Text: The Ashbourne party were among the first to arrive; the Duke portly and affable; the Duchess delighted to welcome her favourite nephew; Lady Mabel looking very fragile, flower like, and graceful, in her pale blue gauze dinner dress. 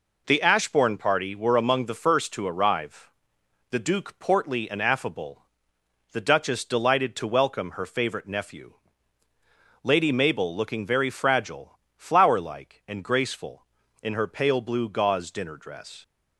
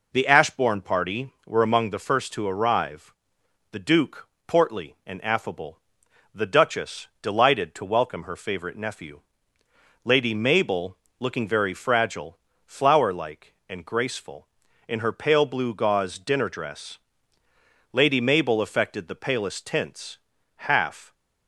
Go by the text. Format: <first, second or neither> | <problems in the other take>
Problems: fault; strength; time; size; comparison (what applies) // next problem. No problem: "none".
first | pauses between "Duke" and "portly"; slight; at 4.2 s; 0.18 s long // pauses between "Mabel" and "looking"; slight; at 10.9 s; 0.22 s long // goes on to say "Lady Mabel affected the palest tints half"; strong; from 17.9 s on; 3.2 s long